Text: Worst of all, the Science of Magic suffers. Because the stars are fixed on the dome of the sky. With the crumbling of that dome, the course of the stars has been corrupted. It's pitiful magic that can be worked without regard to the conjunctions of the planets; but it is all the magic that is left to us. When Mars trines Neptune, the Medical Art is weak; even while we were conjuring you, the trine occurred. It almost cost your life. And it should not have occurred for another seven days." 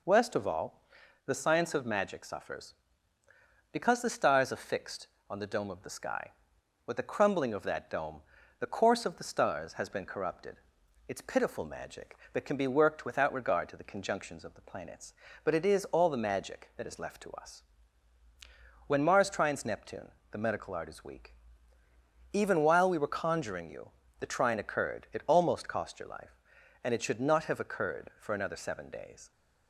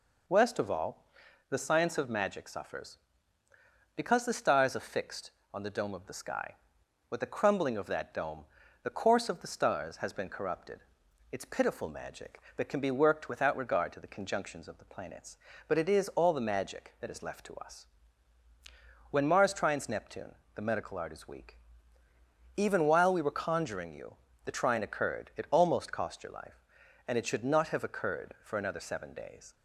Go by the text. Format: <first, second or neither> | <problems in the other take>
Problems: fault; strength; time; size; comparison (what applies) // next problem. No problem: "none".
neither | none